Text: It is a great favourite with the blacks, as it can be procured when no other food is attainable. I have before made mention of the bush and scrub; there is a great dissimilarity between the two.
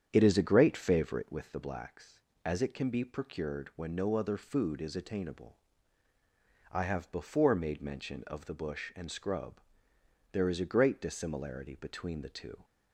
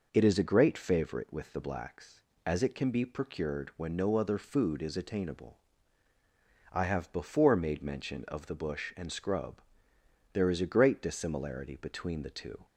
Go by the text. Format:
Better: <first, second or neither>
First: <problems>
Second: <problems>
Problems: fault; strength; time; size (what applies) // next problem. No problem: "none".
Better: second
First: starts louder than the rest; strong; until 1.5 s; 8.5 dB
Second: none